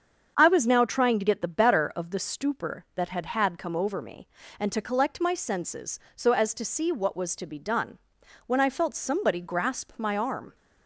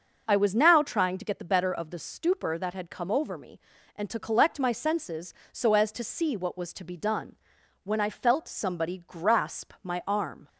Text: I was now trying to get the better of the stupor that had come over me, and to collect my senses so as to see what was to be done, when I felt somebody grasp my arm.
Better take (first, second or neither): second